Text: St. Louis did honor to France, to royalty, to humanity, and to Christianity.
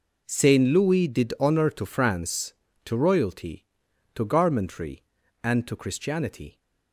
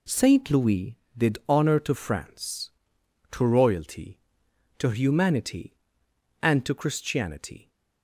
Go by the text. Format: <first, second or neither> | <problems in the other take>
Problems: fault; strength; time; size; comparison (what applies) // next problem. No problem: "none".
second | says "garmentry" for "humanity"; at 4.2 s